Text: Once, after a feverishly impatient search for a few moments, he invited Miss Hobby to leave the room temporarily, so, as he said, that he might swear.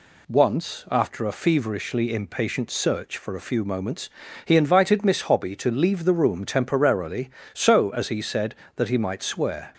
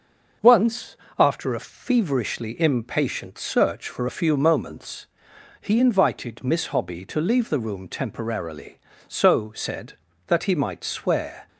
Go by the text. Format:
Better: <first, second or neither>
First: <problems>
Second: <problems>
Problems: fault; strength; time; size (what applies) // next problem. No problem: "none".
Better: first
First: none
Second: starts louder than the rest; noticeable; until 1.6 s; 6 dB // skips "as he"; at 9.5 s